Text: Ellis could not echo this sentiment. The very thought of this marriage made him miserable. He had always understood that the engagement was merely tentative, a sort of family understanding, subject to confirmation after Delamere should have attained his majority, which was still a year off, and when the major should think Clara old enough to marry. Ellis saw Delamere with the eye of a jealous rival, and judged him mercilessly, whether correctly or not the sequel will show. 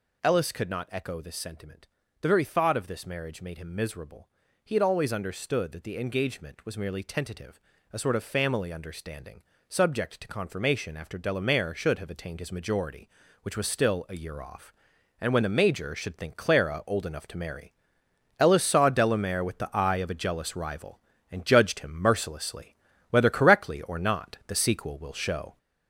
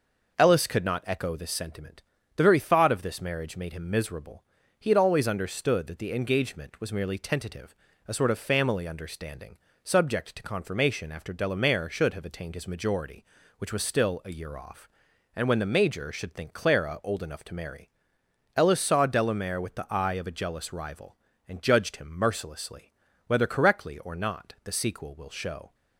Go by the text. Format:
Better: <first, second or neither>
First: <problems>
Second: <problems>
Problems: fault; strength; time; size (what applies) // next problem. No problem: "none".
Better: second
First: gets louder; noticeable; throughout; 5.5 dB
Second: none